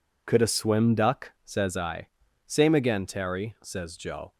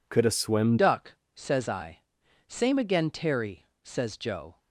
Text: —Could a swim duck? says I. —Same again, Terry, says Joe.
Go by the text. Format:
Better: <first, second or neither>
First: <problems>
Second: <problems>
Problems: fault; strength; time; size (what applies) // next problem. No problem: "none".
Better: first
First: none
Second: changes voice at "duck"; from 0.7 s on; 3.8 s long